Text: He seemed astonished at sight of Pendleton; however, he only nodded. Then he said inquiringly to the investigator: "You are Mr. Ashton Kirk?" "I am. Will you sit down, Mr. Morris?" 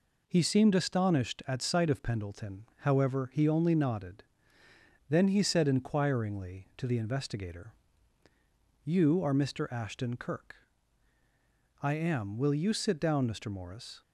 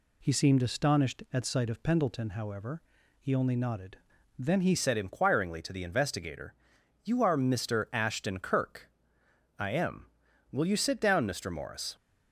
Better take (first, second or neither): first